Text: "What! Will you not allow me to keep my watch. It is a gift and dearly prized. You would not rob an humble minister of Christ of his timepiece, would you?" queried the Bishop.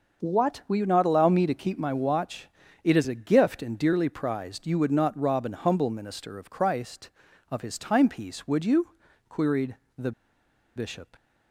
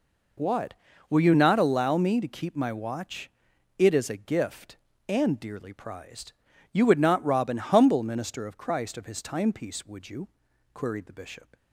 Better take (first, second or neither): second